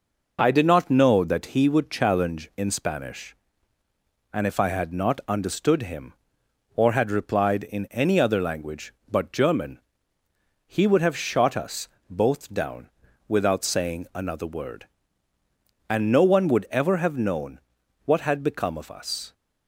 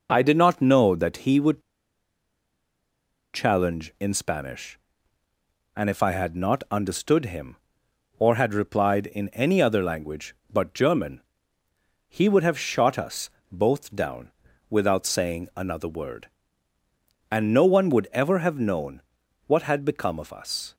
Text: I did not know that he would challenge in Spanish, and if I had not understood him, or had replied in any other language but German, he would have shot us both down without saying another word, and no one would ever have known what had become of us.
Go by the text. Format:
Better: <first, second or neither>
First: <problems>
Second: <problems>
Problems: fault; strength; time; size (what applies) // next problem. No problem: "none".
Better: first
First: pauses between "us" and "both"; slight; at 11.8 s; 0.20 s long // pauses between "down" and "without"; at 12.8 s; 0.40 s long // pauses between "known" and "what"; noticeable; at 17.5 s; 0.46 s long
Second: pauses between "would" and "challenge"; strong; at 1.6 s; 1.7 s long // pauses between "us" and "both"; slight; at 13.3 s; 0.20 s long // pauses between "down" and "without"; at 14.3 s; 0.40 s long // pauses between "known" and "what"; noticeable; at 19.0 s; 0.46 s long